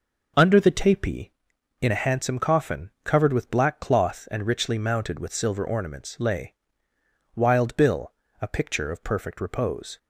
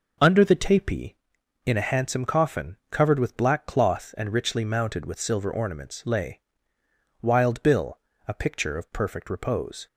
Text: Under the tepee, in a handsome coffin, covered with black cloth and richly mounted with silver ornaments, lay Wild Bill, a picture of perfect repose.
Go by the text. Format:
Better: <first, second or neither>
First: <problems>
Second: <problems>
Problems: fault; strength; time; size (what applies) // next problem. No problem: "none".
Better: neither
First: pauses between "lay" and "Wild"; noticeable; at 6.5 s; 0.82 s long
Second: pauses between "lay" and "Wild"; noticeable; at 6.3 s; 0.82 s long